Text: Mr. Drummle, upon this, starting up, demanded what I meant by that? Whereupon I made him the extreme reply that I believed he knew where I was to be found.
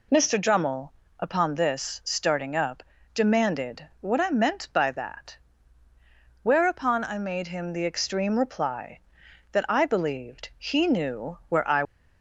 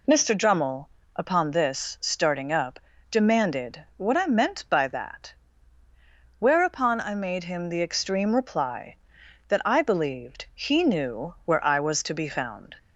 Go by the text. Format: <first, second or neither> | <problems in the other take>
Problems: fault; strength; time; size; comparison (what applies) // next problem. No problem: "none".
second | stops before "was to be found"; at 11.8 s